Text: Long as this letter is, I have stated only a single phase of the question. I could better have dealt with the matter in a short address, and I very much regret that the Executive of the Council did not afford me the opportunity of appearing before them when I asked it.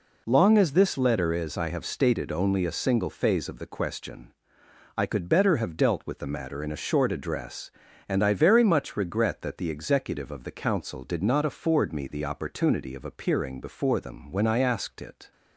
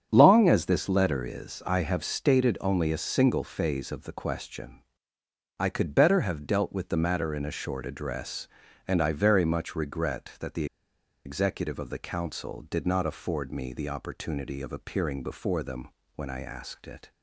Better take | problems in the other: first | starts louder than the rest; strong; until 1.1 s; 8 dB // pauses between "the" and "Executive"; noticeable; at 10.6 s; 0.60 s long // pauses between "them" and "when"; slight; at 15.8 s; 0.30 s long

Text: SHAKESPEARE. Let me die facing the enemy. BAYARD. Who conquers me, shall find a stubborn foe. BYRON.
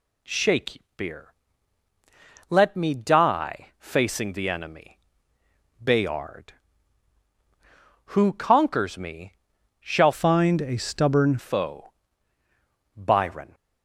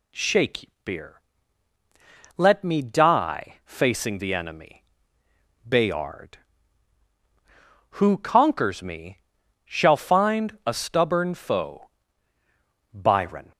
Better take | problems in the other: second | changes voice from "find" to "stubborn"; from 10.1 to 11.3 s; 1.2 s long

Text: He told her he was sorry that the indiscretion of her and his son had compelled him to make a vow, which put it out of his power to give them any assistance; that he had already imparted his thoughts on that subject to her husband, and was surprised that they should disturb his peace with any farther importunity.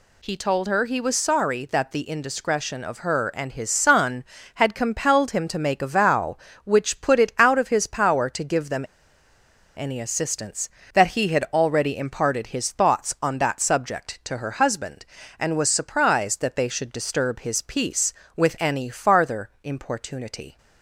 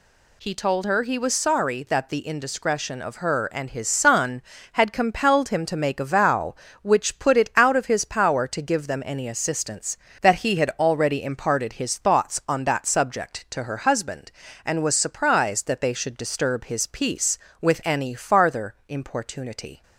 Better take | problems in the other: second | pauses between "them" and "any"; noticeable; at 8.8 s; 0.91 s long

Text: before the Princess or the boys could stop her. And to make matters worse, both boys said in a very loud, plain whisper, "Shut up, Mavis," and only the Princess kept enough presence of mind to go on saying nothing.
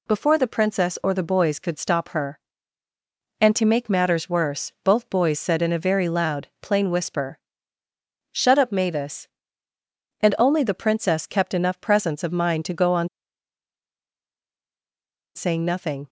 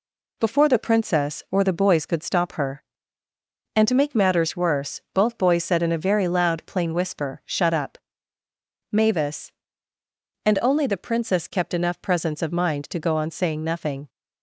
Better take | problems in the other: second | pauses between "on" and "saying"; strong; at 13.0 s; 2.2 s long

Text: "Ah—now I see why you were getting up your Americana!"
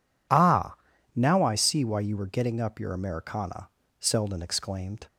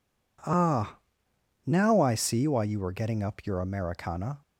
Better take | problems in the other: second | goes on to say "Selden exclaimed"; noticeable; from 3.9 s on; 1.0 s long

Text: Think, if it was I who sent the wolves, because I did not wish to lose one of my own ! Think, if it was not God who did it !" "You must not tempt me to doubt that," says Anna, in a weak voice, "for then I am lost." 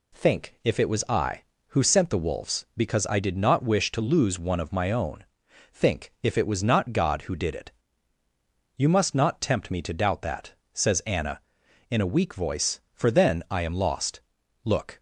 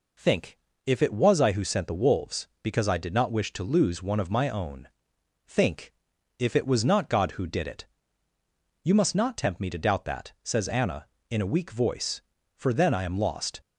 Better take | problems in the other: second | goes on to say "Look"; slight; from 14.6 s on; 0.36 s long

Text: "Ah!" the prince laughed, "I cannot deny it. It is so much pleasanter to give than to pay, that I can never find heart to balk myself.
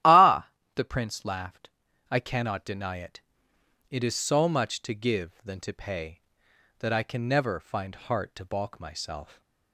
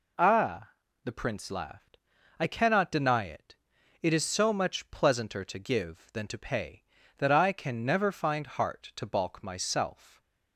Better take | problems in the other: second | starts louder than the rest; strong; until 1.3 s; 13 dB // skips "pleasanter"; at 4.8 s

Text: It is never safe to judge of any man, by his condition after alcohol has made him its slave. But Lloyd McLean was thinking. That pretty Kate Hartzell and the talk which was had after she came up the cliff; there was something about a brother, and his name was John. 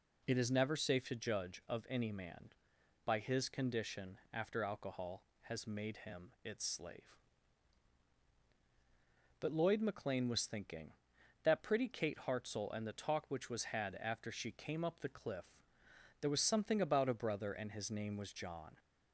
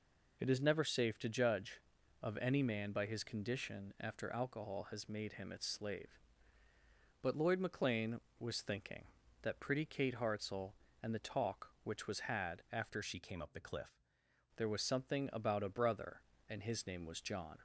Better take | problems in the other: first | changes voice from "she" to "cliff"; from 13.0 to 13.9 s; 0.9 s long

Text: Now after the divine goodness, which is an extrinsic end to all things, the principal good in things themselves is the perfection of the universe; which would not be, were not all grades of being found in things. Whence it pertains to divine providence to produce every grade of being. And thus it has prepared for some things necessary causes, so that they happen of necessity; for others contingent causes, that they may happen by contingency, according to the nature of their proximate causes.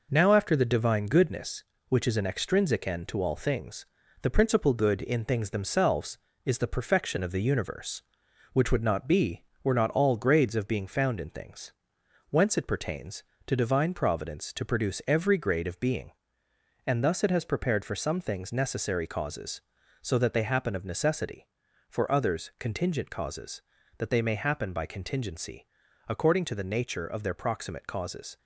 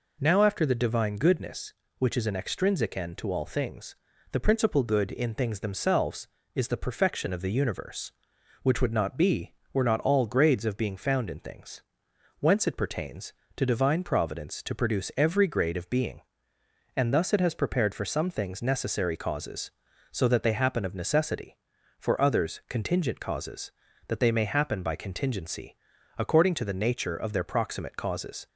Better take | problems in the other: second | gets quieter; noticeable; throughout; 4.5 dB

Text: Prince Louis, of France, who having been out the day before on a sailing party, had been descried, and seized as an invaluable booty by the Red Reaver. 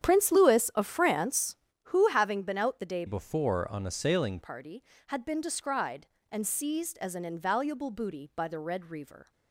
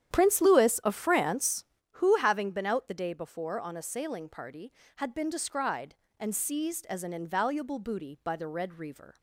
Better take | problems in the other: second | starts louder than the rest; strong; until 1.0 s; 9 dB; strong in the second // changes voice from "before" to "sailing"; from 3.0 to 4.3 s; 1.3 s long

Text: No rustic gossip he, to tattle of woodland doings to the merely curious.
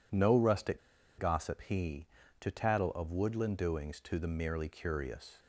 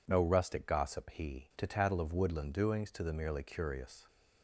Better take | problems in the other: second | pauses between "rustic" and "gossip"; at 0.7 s; 0.39 s long

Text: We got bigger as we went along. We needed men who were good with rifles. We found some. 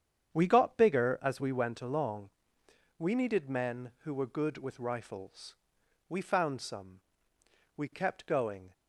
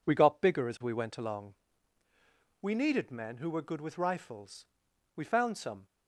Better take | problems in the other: second | starts louder than the rest; strong; until 1.3 s; 8.5 dB // goes on to say "We kept going"; noticeable; from 7.7 s on; 0.97 s long

